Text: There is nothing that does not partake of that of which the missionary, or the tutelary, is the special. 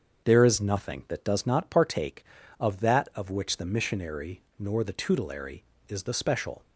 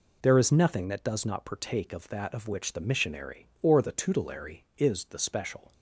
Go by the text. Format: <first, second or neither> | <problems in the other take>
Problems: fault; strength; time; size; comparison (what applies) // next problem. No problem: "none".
second | starts louder than the rest; until 1.3 s; 7 dB // says "nor" for "or"; at 4.5 s